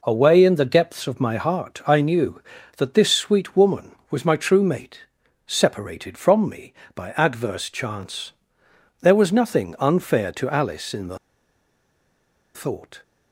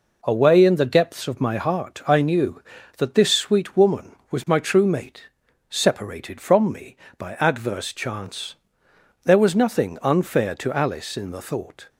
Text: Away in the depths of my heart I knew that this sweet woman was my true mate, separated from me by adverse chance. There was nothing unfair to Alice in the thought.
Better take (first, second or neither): second